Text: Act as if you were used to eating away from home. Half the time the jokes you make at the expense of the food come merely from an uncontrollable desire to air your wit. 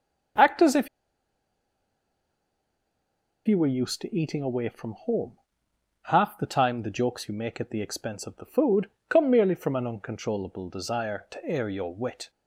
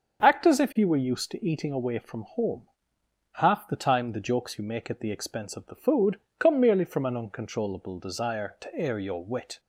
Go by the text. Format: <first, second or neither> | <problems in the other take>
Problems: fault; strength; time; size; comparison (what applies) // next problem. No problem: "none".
second | starts louder than the rest; until 3.9 s; 6.5 dB; also in the second // pauses between "if" and "you"; strong; at 0.8 s; 2.5 s long // pauses between "food" and "come"; slight; at 8.8 s; 0.20 s long; slight in the second